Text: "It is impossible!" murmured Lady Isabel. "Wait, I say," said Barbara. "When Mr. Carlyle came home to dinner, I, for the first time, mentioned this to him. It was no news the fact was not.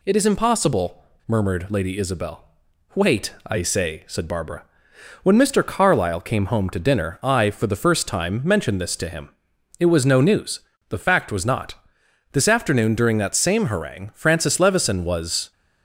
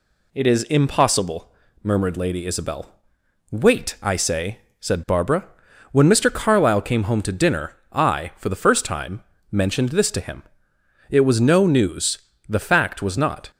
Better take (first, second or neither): second